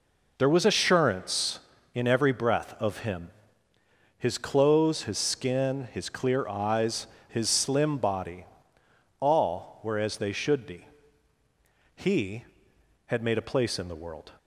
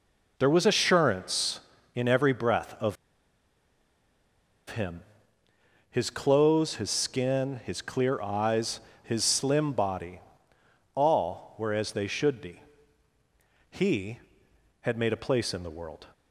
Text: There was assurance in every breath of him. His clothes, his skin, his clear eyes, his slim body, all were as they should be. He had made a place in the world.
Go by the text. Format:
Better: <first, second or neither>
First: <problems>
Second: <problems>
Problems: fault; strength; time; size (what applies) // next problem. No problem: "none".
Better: first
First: none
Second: pauses between "of" and "him"; strong; at 2.9 s; 1.7 s long